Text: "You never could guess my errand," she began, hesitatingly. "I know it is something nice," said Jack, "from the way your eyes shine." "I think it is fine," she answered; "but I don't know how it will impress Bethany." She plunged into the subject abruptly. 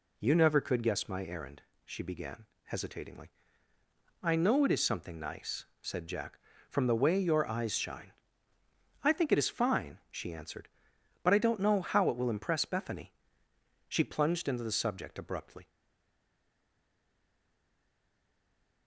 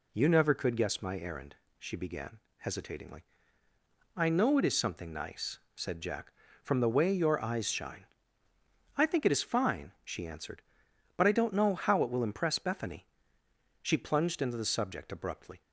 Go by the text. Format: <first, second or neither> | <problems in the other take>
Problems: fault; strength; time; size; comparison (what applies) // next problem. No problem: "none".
second | stays silent after the last word; strong; from 15.6 s on; 3.2 s long